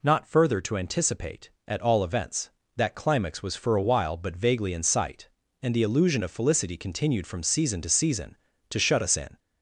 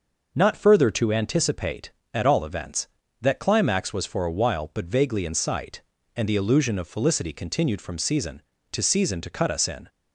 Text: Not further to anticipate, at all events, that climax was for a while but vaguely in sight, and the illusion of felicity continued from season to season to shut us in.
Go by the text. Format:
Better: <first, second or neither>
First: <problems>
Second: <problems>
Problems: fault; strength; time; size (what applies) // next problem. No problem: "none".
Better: first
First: none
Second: says "cut" for "shut"; at 9.3 s